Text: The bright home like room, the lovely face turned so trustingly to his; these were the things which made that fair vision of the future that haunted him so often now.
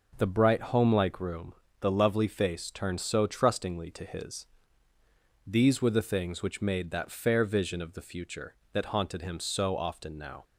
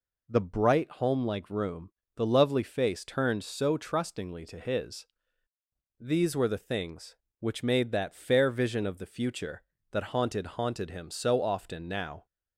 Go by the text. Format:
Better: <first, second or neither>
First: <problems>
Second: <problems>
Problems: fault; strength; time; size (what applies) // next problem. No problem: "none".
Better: first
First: none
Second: says "haunted" twice; at 10.4 s